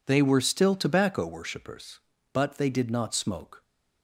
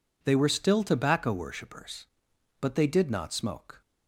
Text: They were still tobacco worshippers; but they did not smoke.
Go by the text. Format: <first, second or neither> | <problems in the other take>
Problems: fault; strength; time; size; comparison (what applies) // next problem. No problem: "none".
neither | none